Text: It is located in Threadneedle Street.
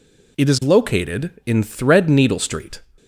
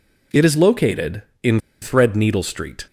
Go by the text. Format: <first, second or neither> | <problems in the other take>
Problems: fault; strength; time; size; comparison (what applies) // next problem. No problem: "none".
first | pauses between "in" and "Threadneedle"; slight; at 1.5 s; 0.23 s long